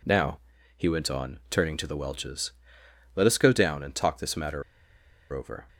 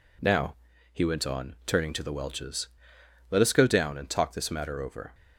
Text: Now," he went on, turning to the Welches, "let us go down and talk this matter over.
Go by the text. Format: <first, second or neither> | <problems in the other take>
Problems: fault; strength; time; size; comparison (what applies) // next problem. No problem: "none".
second | pauses between "matter" and "over"; noticeable; at 4.6 s; 0.70 s long